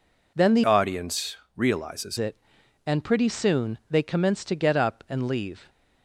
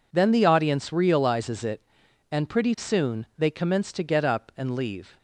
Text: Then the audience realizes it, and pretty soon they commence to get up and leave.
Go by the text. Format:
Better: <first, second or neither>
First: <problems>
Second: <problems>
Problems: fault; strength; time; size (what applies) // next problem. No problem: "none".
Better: second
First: changes voice from "audience" to "realizes"; from 0.6 to 2.1 s; 1.5 s long // pauses between "audience" and "realizes"; slight; at 1.3 s; 0.20 s long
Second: none